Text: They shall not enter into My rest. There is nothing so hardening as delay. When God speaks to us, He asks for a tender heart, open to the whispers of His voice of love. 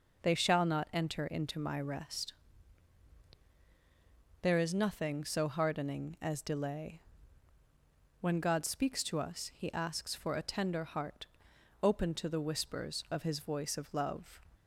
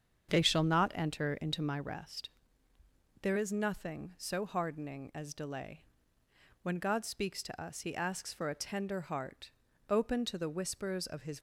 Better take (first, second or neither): first